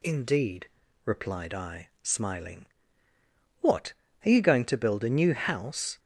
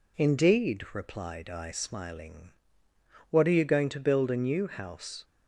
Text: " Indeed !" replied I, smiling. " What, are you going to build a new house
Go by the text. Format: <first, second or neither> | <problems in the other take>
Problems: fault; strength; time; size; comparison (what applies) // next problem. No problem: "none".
neither | none